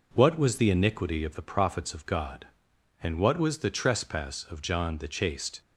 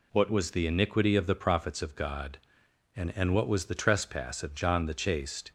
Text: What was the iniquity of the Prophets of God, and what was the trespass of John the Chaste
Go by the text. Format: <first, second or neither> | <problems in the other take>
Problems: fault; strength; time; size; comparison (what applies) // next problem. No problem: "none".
first | says "and" twice; at 3.1 s